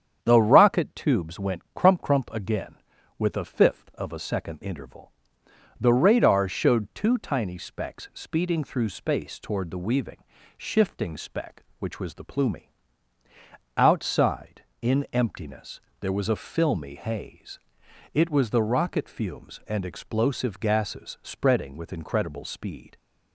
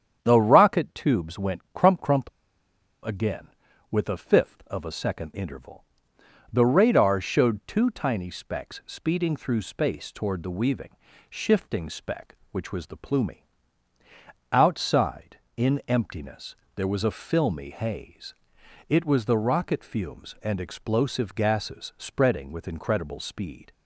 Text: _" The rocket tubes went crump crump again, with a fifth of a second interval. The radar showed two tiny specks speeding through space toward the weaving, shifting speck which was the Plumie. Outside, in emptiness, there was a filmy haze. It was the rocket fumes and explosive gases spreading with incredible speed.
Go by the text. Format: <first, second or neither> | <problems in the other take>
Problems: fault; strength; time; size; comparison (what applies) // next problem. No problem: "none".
first | starts louder than the rest; strong; until 1.2 s; 8.5 dB; strong in the first // pauses between "crump" and "again"; noticeable; at 2.2 s; 0.74 s long